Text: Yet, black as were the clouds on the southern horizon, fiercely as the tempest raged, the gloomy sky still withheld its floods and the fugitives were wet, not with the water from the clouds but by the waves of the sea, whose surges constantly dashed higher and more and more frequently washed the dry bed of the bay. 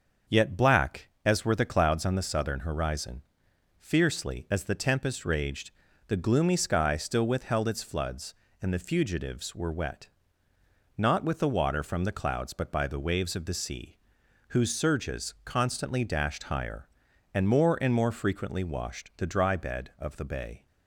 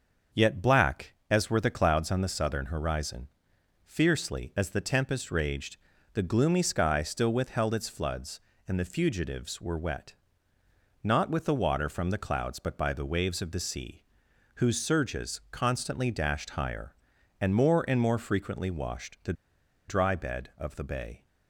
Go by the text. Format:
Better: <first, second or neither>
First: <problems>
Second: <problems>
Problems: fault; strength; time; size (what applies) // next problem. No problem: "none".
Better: first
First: starts louder than the rest; until 1.4 s; 6.5 dB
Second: starts louder than the rest; until 1.4 s; 6.5 dB // pauses between "the" and "dry"; noticeable; at 19.3 s; 0.55 s long